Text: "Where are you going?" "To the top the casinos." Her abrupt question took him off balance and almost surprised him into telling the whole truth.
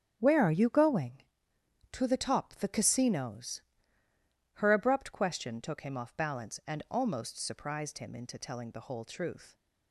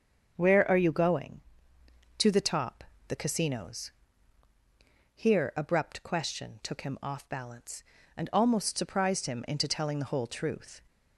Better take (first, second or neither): first